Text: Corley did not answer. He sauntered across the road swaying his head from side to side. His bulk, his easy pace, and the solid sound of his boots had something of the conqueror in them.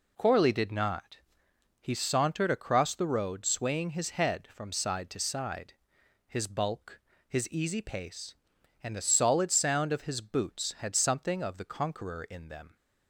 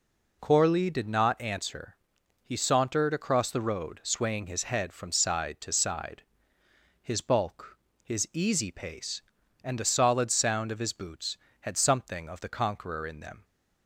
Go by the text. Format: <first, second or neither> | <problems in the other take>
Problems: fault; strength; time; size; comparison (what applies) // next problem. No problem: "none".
second | skips "answer"; at 1.4 s